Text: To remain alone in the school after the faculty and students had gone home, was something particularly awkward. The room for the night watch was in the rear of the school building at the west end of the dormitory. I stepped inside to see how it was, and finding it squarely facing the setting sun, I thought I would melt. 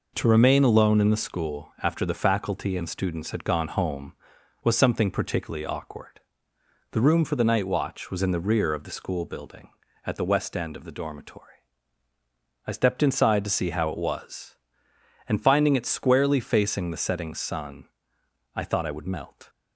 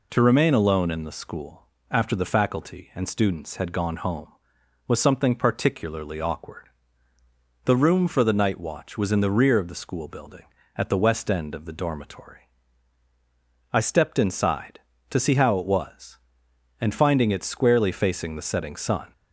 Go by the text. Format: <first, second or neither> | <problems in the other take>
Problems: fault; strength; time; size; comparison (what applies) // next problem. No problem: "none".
first | pauses between "school" and "after"; slight; at 1.6 s; 0.24 s long // stops before "I thought I would melt"; at 19.1 s